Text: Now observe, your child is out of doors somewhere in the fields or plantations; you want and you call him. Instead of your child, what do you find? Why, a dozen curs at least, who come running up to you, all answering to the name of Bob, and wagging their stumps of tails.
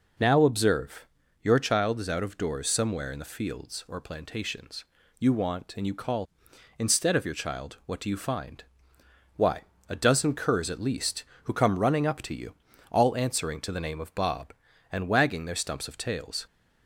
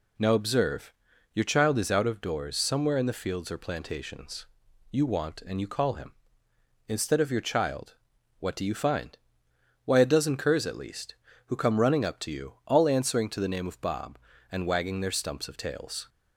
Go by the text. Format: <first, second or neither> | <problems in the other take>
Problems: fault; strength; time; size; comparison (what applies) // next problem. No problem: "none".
second | skips "him"; at 6.5 s